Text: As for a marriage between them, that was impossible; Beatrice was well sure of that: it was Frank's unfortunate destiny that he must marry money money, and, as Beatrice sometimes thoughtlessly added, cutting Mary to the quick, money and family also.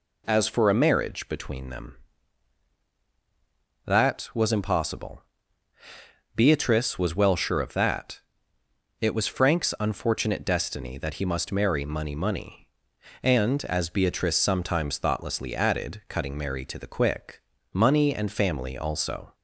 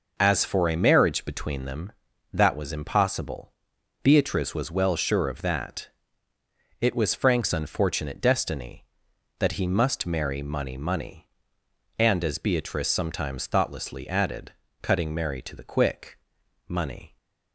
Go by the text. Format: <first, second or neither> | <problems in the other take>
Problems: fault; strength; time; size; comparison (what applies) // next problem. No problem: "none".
first | stops before "and family also"; at 17.1 s